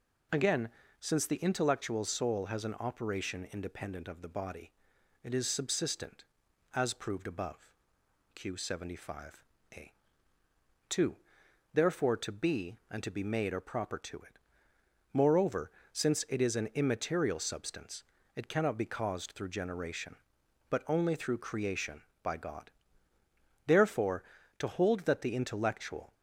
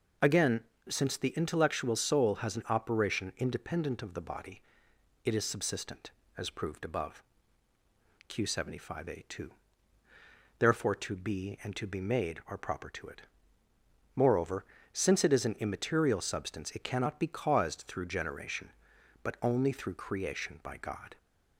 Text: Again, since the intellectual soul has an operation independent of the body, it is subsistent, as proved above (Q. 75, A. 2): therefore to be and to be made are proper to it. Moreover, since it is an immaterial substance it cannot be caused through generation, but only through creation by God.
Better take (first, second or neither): second